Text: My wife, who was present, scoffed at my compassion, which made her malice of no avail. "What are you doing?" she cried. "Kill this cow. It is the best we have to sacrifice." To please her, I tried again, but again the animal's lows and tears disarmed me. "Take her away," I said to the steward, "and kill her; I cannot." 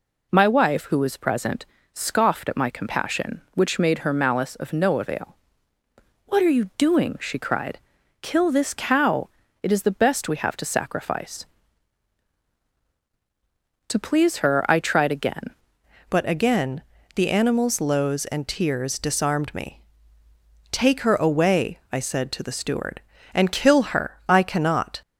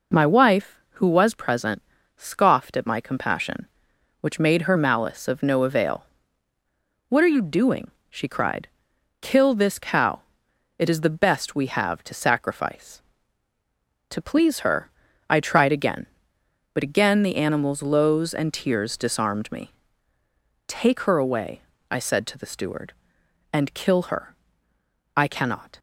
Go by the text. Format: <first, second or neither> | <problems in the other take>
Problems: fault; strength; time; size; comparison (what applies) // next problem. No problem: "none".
second | changes voice at "but"; from 16.1 s on; 8.9 s long // pauses between "again" and "the"; slight; at 16.8 s; 0.32 s long